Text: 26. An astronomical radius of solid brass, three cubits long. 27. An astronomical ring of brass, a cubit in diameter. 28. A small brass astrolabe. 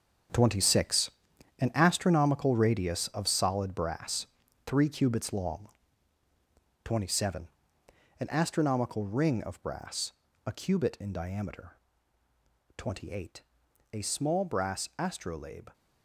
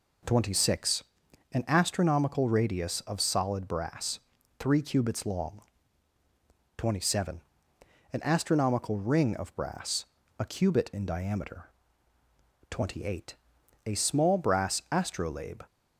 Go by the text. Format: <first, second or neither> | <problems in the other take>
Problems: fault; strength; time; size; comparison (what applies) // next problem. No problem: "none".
second | gets quieter; strong; throughout; 10.5 dB